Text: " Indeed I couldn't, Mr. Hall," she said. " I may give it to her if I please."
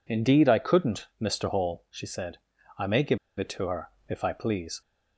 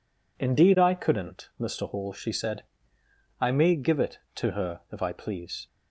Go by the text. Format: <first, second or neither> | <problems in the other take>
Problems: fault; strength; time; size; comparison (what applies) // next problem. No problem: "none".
second | pauses between "give" and "it"; slight; at 3.1 s; 0.20 s long // pauses between "her" and "if"; slight; at 3.9 s; 0.18 s long